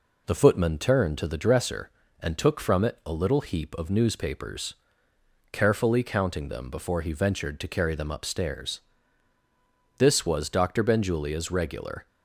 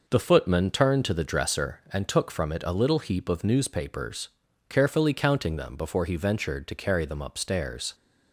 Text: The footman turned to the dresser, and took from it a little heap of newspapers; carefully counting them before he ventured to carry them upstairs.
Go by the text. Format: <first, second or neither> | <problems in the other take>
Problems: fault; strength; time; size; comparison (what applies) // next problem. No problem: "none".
second | goes on to say "This was Doctor Benjulia's regular"; strong; from 9.9 s on; 2.0 s long